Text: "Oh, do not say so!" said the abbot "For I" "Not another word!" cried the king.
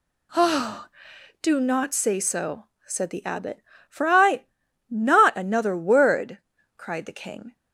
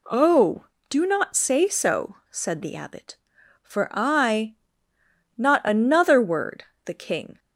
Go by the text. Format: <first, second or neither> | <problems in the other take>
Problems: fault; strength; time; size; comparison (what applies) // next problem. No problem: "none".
first | pauses between "I" and "Not"; noticeable; at 4.5 s; 0.80 s long; also in the first // skips "cried"; at 6.7 s